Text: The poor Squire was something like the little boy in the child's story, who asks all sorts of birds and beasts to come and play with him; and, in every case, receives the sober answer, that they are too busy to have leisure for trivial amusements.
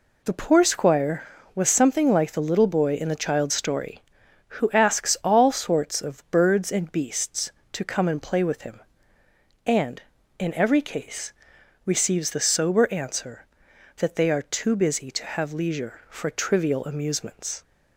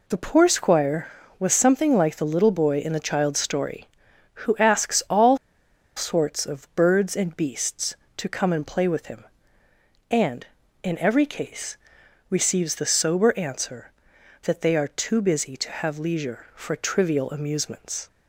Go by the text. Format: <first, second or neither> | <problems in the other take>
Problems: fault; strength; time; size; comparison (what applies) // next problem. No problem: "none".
first | pauses between "all" and "sorts"; noticeable; at 5.3 s; 0.59 s long